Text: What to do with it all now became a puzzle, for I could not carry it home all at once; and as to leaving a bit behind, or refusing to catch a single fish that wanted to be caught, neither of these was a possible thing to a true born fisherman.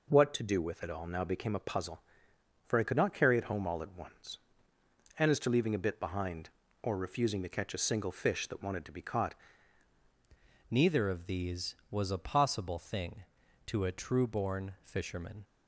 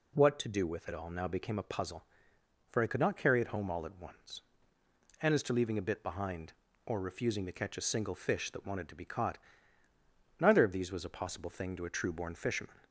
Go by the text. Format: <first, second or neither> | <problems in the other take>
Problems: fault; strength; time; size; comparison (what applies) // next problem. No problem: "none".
second | changes voice at "neither"; from 10.7 s on; 4.7 s long